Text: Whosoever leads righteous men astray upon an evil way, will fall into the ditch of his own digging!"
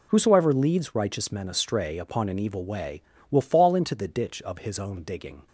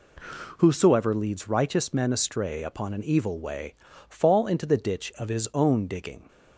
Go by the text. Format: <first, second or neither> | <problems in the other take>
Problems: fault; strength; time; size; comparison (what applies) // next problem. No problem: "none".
first | skips "will"; at 3.9 s